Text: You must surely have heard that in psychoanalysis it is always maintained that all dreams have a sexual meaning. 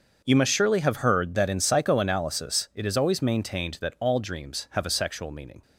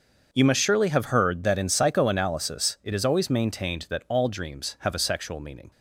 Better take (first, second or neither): neither